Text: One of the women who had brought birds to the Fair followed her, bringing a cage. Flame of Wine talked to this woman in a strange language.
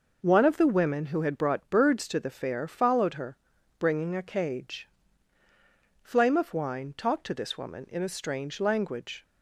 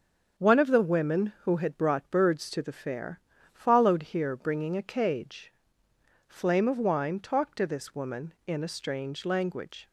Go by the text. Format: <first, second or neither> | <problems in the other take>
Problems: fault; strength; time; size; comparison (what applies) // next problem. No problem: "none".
first | starts louder than the rest; until 1.5 s; 6.5 dB // pauses between "Fair" and "followed"; slight; at 3.2 s; 0.32 s long // says "here" for "her"; at 4.0 s